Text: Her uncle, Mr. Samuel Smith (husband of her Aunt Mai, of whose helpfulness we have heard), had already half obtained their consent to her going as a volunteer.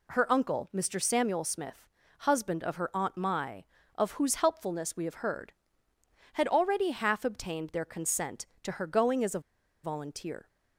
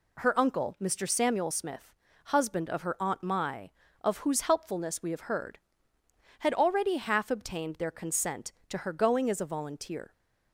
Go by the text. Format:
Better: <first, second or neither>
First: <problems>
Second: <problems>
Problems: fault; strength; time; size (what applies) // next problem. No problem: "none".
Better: second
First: pauses between "a" and "volunteer"; at 9.3 s; 0.43 s long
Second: none